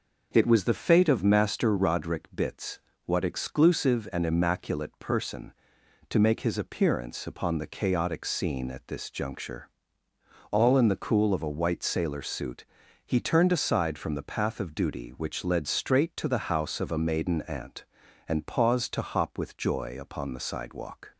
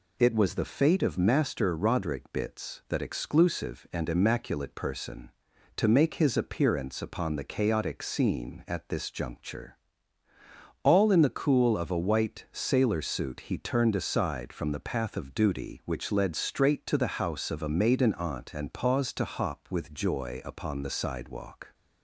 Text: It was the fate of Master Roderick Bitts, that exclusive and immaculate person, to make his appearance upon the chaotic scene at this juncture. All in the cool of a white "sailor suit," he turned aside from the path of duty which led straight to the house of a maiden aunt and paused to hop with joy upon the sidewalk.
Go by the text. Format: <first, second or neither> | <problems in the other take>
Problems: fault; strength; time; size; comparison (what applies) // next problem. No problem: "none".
second | starts louder than the rest; noticeable; until 1.3 s; 6 dB // says "what" for "that"; at 3.0 s